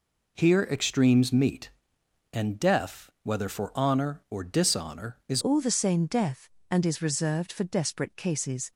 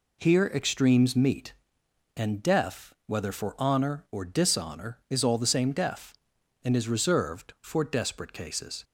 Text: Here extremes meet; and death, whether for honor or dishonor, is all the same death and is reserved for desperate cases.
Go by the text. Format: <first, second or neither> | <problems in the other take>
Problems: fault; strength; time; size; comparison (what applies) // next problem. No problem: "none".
second | changes voice at "all"; from 5.3 s on; 3.4 s long